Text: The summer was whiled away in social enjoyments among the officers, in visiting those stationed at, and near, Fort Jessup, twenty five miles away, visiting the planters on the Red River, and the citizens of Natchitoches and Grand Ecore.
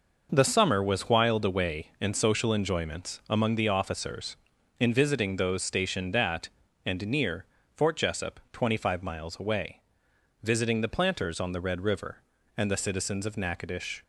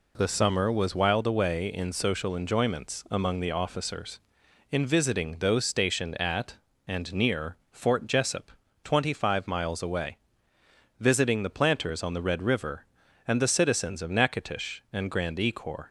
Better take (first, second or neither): second